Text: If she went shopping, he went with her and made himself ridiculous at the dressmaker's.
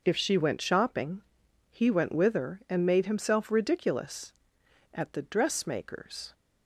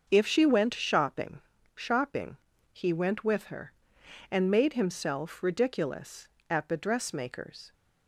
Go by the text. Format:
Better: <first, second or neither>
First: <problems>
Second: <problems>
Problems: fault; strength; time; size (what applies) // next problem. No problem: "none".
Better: first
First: none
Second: starts louder than the rest; until 1.1 s; 6.5 dB // says "shopping" twice; at 1.7 s